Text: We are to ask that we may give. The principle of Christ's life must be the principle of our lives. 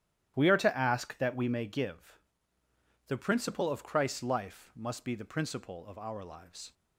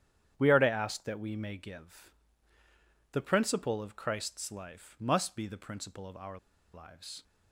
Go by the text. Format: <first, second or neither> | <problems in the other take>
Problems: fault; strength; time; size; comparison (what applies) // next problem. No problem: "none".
first | starts louder than the rest; strong; until 1.3 s; 9.5 dB; strong in the first // pauses between "our" and "lives"; at 6.3 s; 0.36 s long